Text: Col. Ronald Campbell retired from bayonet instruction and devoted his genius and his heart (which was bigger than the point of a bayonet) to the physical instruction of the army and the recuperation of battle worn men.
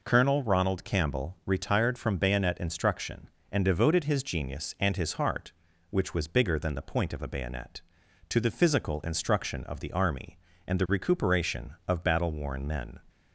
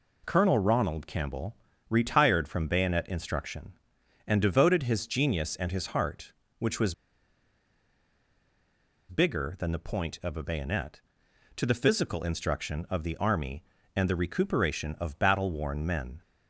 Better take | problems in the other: first | pauses between "Campbell" and "retired"; slight; at 1.5 s; 0.36 s long // pauses between "was" and "bigger"; strong; at 6.9 s; 2.1 s long

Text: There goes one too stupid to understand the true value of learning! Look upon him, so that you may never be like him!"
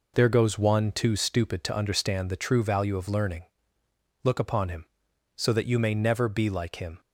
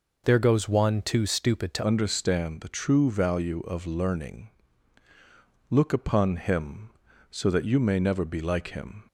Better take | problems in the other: first | changes voice at "understand"; from 1.8 s on; 7.2 s long

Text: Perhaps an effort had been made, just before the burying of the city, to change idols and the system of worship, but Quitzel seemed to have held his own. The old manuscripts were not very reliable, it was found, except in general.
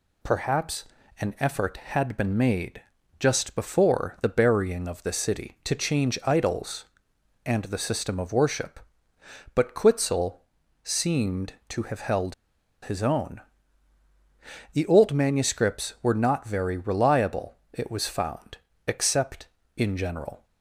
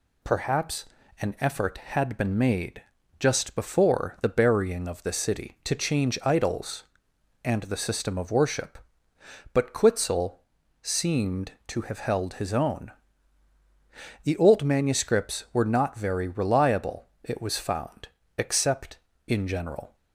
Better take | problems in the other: second | pauses between "Perhaps" and "an"; slight; at 0.8 s; 0.36 s long; slight in the second // pauses between "Quitzel" and "seemed"; at 10.4 s; 0.44 s long; also in the second // pauses between "held" and "his"; noticeable; at 12.3 s; 0.50 s long

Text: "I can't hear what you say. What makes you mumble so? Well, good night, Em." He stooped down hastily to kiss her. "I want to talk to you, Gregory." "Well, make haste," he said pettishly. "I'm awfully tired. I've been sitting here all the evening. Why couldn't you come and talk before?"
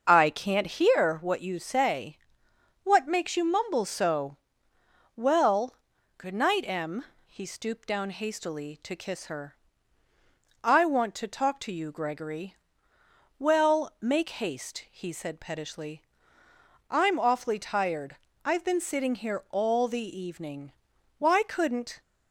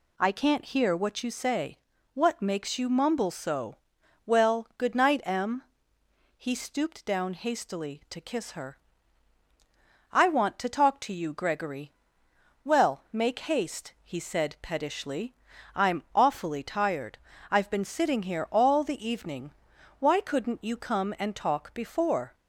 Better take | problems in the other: second | starts louder than the rest; until 1.0 s; 6.5 dB // stops before "you come and talk before"; at 22.0 s

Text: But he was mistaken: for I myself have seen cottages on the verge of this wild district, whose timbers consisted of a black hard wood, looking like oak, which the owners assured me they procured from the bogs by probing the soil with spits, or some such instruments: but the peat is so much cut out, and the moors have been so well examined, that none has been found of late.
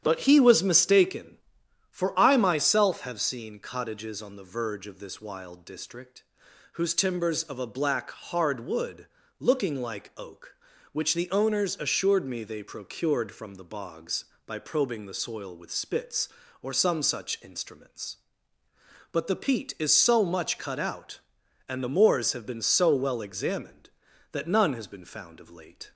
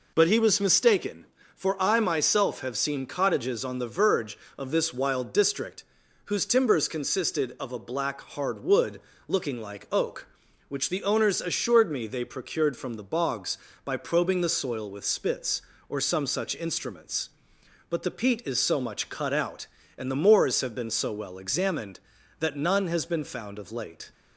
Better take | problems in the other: second | starts louder than the rest; strong; until 1.0 s; 9.5 dB // skips "consisted"; at 7.4 s

